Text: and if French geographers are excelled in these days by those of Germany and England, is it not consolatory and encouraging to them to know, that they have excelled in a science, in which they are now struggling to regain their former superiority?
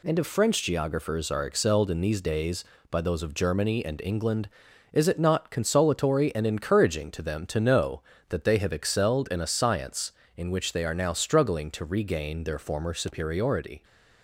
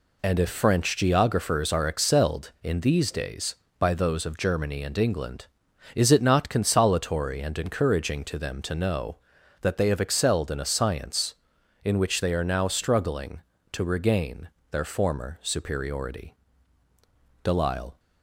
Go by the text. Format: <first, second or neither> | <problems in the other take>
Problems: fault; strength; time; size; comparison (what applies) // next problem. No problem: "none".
first | pauses between "regain" and "their"; slight; at 14.4 s; 0.22 s long // goes on to say "Delisle"; from 17.4 s on; 0.56 s long